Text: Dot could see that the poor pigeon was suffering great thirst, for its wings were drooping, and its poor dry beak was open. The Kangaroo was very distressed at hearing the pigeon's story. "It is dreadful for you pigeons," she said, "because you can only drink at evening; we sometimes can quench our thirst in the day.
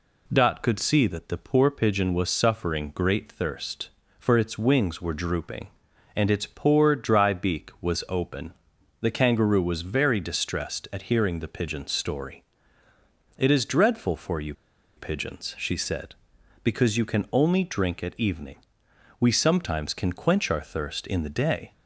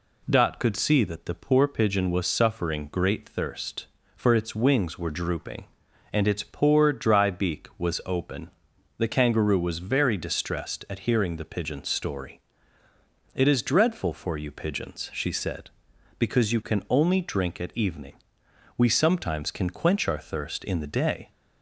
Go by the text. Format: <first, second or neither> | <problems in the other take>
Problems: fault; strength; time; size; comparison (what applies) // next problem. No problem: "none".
second | pauses between "you" and "pigeons"; at 14.5 s; 0.44 s long